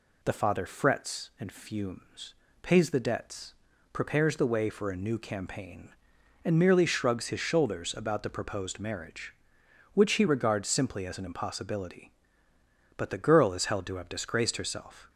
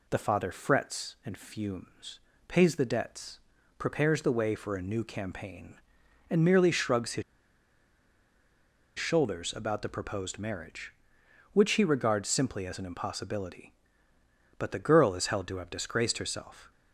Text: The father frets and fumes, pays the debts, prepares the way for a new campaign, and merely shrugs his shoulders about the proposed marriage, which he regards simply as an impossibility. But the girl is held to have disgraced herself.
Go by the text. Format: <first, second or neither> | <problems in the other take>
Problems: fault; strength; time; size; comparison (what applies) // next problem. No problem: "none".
first | pauses between "his" and "shoulders"; strong; at 7.2 s; 1.7 s long